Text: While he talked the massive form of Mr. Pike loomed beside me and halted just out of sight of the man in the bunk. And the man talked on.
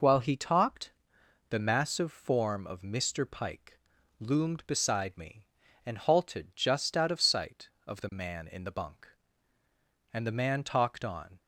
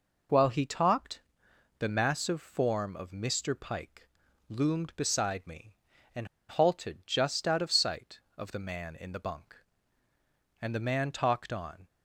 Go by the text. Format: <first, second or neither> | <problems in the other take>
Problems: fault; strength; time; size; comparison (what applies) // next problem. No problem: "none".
first | pauses between "talked" and "the"; noticeable; at 1.2 s; 0.58 s long; noticeable in the first // pauses between "Pike" and "loomed"; at 4.0 s; 0.42 s long; also in the first // pauses between "and" and "halted"; slight; at 6.2 s; 0.24 s long